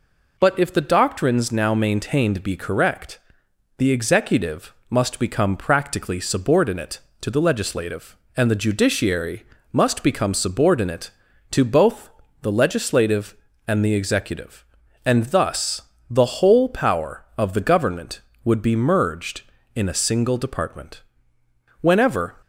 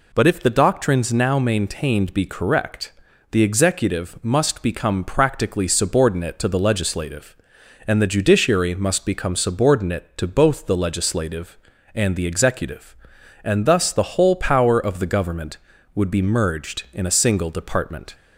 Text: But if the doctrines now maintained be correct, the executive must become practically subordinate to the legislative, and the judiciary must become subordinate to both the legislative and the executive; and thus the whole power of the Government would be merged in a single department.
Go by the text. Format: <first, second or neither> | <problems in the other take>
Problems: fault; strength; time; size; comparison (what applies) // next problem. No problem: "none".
second | pauses between "executive" and "must"; slight; at 4.7 s; 0.16 s long // pauses between "judiciary" and "must"; slight; at 9.4 s; 0.26 s long // pauses between "both" and "the"; slight; at 12.0 s; 0.32 s long // pauses between "thus" and "the"; slight; at 15.8 s; 0.27 s long // goes on to say "Whenever"; from 21.8 s on; 0.56 s long